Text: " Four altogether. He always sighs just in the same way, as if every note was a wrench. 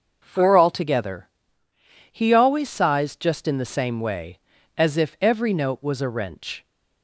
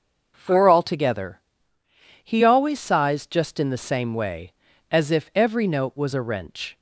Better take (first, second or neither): neither